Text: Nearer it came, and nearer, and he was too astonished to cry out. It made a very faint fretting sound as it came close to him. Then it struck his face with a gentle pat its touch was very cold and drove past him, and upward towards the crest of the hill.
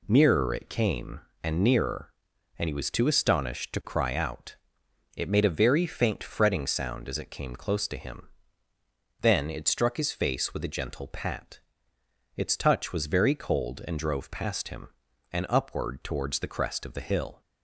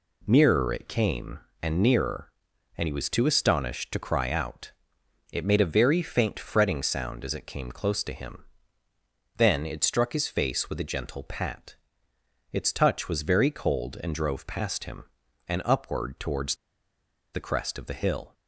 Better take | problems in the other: first | pauses between "pat" and "its"; noticeable; at 11.7 s; 0.76 s long; noticeable in the first // pauses between "towards" and "the"; noticeable; at 16.5 s; 0.77 s long

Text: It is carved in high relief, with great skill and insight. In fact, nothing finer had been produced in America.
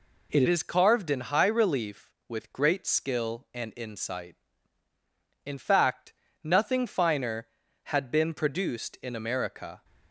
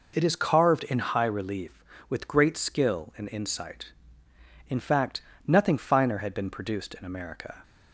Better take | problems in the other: second | changes voice at "is"; from 0.4 s on; 9.4 s long

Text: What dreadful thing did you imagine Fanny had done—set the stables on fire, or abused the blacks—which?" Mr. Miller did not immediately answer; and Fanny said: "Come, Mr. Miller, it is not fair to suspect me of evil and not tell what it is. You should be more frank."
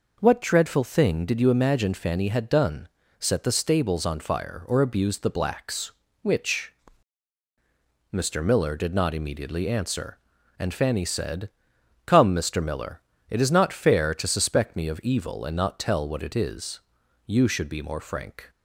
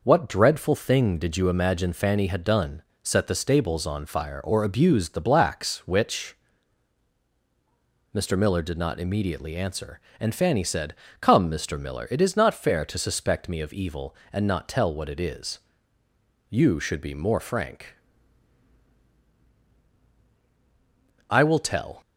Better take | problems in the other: first | goes on to say "I will tell"; noticeable; from 21.3 s on; 0.70 s long

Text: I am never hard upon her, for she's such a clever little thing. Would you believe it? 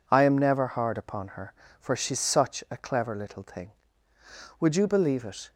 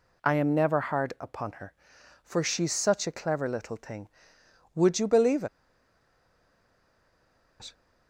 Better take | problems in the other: first | pauses between "believe" and "it"; strong; at 5.4 s; 2.1 s long

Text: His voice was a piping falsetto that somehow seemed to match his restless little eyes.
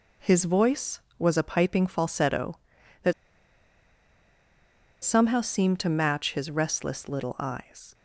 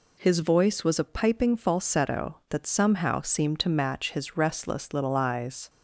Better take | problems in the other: second | pauses between "that" and "somehow"; strong; at 3.1 s; 1.9 s long

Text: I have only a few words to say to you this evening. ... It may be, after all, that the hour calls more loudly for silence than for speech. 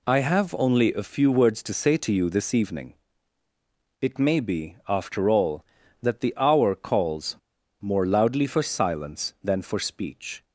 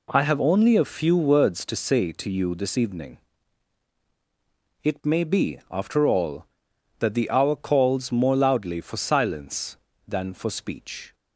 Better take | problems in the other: second | pauses between "calls" and "more"; at 7.3 s; 0.43 s long

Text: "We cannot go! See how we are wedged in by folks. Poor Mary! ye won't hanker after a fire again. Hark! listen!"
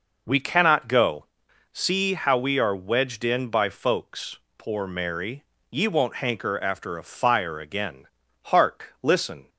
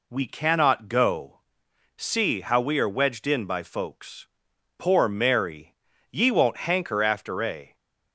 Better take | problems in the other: first | stops before "fire again Hark listen"; at 7.7 s

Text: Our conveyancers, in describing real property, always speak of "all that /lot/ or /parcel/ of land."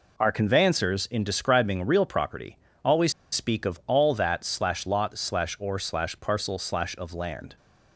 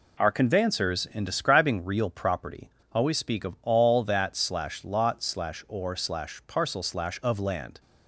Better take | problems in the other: second | pauses between "always" and "speak"; slight; at 3.1 s; 0.20 s long

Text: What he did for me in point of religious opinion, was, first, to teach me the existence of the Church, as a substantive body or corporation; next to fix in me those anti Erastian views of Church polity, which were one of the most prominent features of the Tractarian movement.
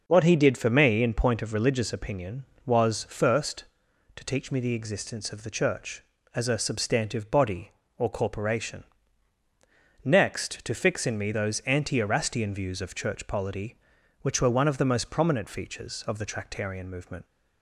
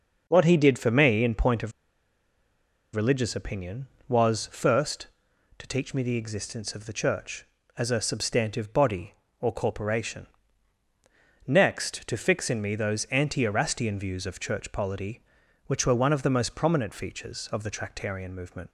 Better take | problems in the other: first | starts louder than the rest; until 1.2 s; 6 dB; noticeable in the first // pauses between "of" and "religious"; at 1.7 s; 1.2 s long

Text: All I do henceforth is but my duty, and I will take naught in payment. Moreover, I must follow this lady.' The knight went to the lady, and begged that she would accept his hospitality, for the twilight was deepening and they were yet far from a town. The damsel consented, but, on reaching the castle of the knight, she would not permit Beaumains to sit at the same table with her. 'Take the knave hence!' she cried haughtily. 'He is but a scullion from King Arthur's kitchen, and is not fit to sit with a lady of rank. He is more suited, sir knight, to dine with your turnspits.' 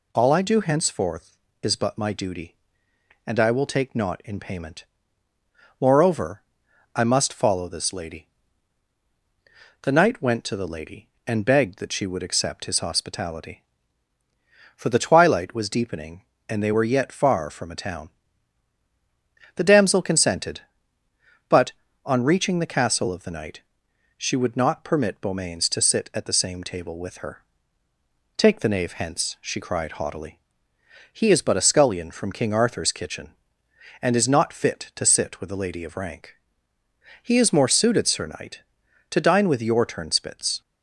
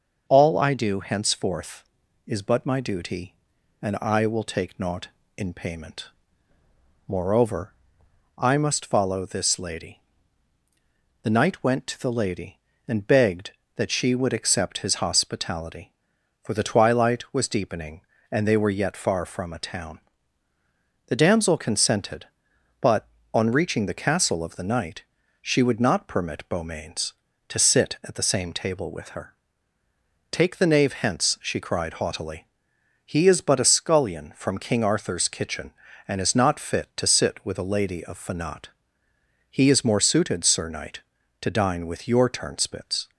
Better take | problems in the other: first | starts louder than the rest; until 1.2 s; 6.5 dB // says "fanat" for "rank"; at 38.1 s

